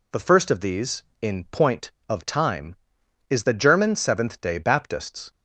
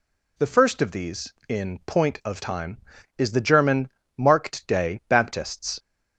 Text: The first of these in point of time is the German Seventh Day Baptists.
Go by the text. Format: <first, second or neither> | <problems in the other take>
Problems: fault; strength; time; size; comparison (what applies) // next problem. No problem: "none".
first | says "Marked" for "Seventh"; at 4.1 s